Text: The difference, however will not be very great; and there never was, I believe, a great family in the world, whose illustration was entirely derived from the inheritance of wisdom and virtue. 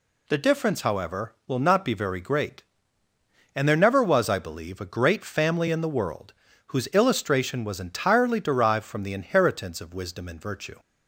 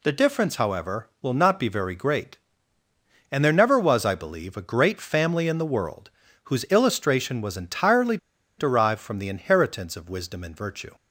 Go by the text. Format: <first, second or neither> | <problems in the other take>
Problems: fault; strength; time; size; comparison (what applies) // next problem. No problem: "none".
first | pauses between "entirely" and "derived"; at 8.1 s; 0.41 s long